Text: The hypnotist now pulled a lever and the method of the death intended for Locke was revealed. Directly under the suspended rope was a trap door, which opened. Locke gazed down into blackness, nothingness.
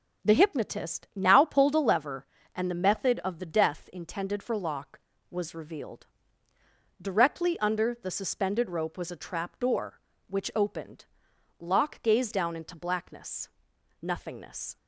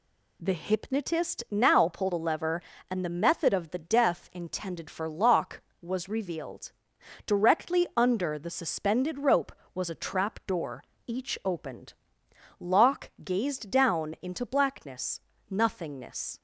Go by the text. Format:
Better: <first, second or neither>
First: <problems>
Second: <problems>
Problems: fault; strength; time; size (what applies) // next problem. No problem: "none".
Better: first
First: none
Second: says "each" for "which"; at 11.0 s